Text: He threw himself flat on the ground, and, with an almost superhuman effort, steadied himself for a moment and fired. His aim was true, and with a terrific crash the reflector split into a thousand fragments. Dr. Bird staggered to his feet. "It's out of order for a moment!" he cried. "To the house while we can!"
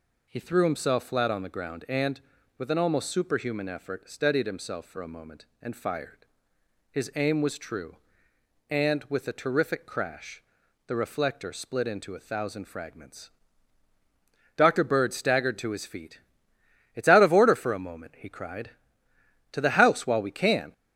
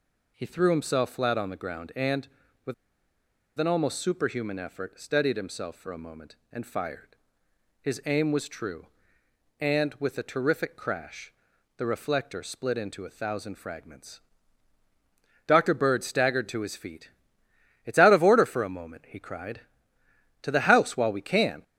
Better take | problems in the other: first | pauses between "with" and "an"; noticeable; at 2.7 s; 0.84 s long // pauses between "crash" and "the"; noticeable; at 11.3 s; 0.46 s long; noticeable in the first

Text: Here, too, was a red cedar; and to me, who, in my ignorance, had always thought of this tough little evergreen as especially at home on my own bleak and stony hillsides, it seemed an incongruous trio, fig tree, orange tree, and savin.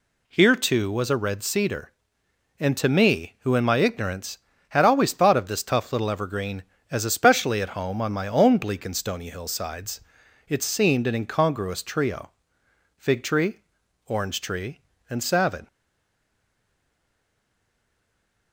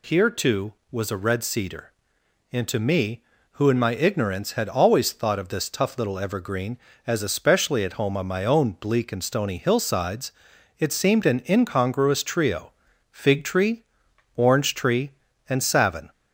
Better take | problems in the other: second | stays silent after the last word; strong; from 15.6 s on; 2.9 s long

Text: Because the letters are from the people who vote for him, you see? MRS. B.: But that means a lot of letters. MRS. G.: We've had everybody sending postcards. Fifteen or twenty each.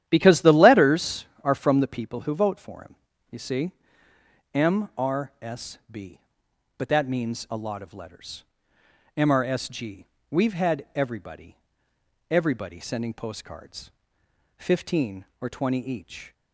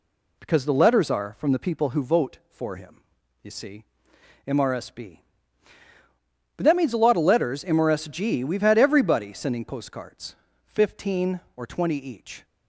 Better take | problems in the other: second | starts louder than the rest; strong; until 1.0 s; 11.5 dB // says "everybody" twice; at 12.3 s

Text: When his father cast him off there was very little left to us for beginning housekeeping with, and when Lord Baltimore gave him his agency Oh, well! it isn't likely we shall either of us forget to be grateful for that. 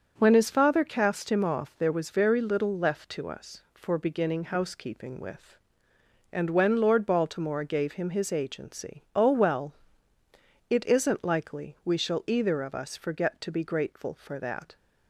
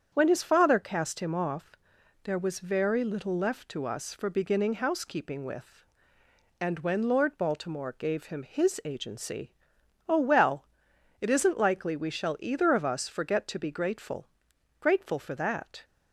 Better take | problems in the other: first | starts louder than the rest; strong; until 1.1 s; 8 dB; also in the first // pauses between "off" and "there"; noticeable; at 1.7 s; 0.50 s long // pauses between "agency" and "Oh"; noticeable; at 9.5 s; 0.54 s long // says "grateful" twice; at 14.8 s

